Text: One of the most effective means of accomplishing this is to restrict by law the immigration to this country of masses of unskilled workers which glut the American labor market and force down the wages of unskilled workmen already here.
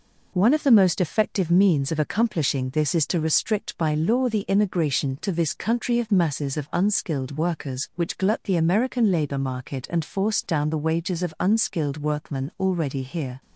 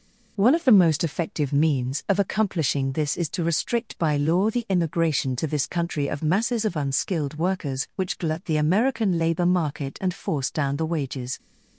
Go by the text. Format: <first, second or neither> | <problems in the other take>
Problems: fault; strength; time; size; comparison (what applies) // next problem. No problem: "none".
first | stops before "of unskilled workmen already here"; at 11.3 s